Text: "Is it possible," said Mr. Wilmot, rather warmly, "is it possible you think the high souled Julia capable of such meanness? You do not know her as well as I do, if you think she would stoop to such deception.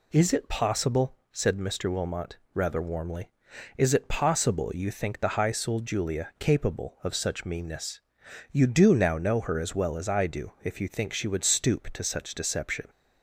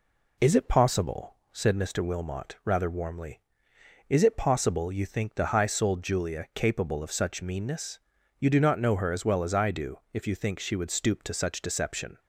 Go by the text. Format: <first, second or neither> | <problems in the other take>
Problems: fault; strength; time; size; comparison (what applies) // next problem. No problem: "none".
second | says "now" for "not"; at 8.9 s